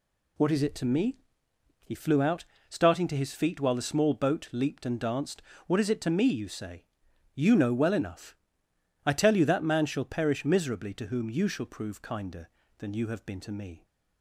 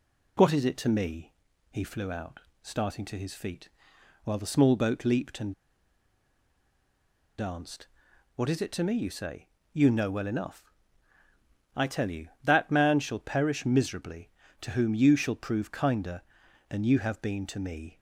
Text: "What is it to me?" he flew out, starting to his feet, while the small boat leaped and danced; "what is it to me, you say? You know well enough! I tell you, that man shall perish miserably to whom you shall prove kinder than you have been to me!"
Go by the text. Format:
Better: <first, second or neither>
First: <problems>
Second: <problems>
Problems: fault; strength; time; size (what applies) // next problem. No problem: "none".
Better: first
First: none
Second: pauses between "and" and "danced"; strong; at 5.5 s; 1.8 s long